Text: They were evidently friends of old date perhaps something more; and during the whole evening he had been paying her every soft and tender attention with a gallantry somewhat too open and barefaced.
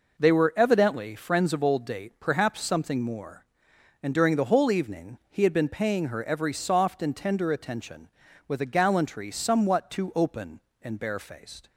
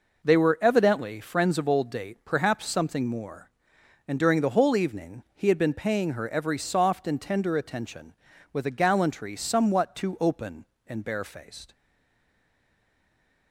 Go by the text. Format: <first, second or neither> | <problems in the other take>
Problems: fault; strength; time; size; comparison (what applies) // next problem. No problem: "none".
first | stays silent after the last word; noticeable; from 11.7 s on; 1.8 s long